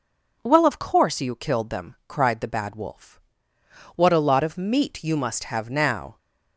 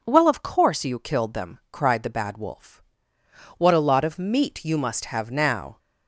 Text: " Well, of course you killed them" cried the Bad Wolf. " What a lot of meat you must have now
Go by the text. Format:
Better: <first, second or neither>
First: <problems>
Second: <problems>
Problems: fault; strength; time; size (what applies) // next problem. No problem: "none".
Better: neither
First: none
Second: none